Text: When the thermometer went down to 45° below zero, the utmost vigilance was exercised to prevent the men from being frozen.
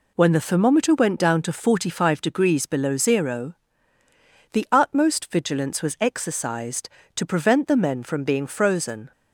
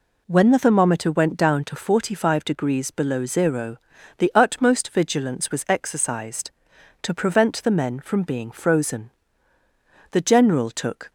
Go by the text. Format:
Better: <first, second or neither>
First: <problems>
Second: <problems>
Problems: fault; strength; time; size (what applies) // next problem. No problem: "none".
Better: first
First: none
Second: goes on to say "The general took"; noticeable; from 10.1 s on; 0.98 s long